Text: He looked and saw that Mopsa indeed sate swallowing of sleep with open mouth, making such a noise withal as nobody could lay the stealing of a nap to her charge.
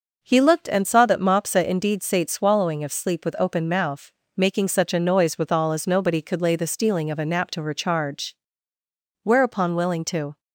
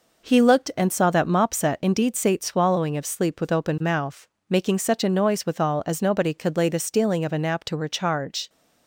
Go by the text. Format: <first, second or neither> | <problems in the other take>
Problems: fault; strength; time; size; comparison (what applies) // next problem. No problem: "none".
second | goes on to say "Whereupon willing to"; noticeable; from 9.2 s on; 1.1 s long